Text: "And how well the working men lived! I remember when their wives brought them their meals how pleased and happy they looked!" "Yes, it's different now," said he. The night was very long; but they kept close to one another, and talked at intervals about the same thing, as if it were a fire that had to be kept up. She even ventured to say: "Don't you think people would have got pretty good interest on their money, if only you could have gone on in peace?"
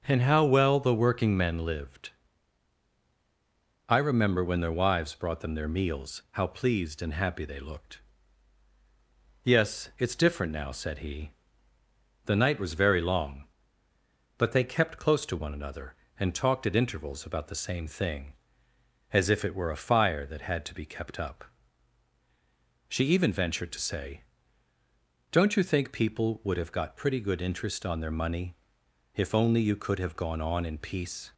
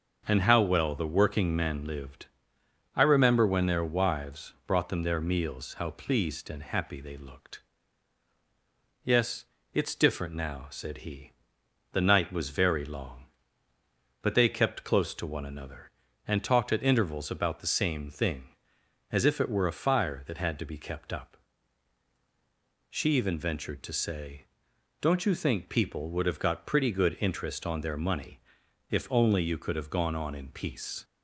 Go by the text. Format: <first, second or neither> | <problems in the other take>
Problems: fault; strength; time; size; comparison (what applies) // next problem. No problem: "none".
neither | starts louder than the rest; the same in both